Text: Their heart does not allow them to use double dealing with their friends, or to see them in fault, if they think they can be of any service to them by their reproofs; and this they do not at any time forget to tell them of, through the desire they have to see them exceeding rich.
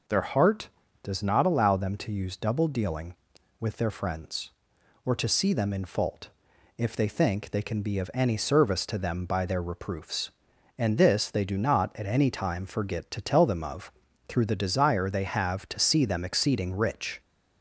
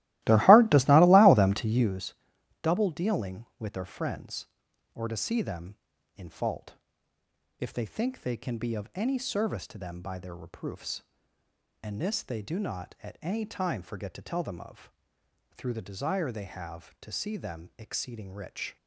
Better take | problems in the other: first | starts louder than the rest; strong; until 2.0 s; 17 dB // pauses between "use" and "double"; noticeable; at 2.1 s; 0.48 s long

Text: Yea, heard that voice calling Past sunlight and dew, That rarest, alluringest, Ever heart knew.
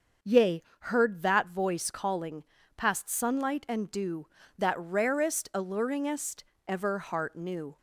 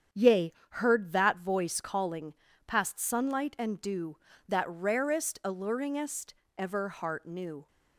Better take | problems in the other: first | gets quieter; throughout; 6 dB // starts louder than the rest; strong; until 1.3 s; 8 dB; also in the first // pauses between "calling" and "Past"; slight; at 2.3 s; 0.34 s long; slight in the first

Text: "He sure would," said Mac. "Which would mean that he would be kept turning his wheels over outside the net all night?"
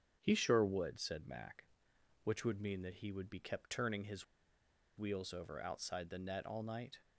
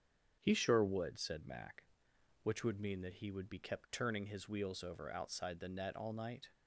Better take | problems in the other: second | starts louder than the rest; strong; until 1.2 s; 7.5 dB; strong in the second // pauses between "his" and "wheels"; noticeable; at 4.2 s; 0.73 s long

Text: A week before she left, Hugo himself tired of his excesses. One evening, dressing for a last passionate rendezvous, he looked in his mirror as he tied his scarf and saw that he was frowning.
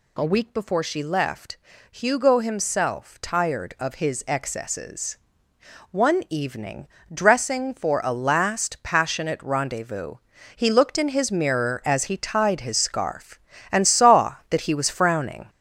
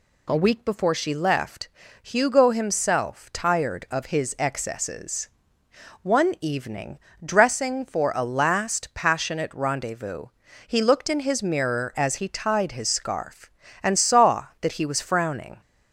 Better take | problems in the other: second | gets louder; noticeable; throughout; 5.5 dB

